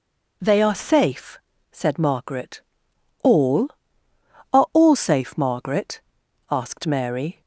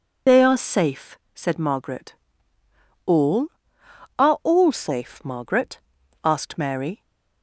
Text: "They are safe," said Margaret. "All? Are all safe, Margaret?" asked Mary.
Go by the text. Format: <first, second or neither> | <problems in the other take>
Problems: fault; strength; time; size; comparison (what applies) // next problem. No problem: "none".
first | loses the start of "They"; at 0.2 s; 50 ms